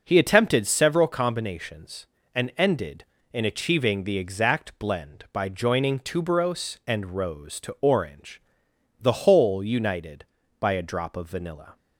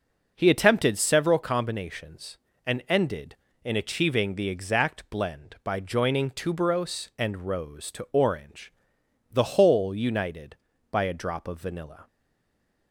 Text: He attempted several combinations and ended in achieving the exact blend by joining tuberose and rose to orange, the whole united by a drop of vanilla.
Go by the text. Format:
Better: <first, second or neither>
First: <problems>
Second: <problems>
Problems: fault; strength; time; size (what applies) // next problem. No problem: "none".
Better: first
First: none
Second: stays silent after the last word; slight; from 12.0 s on; 0.9 s long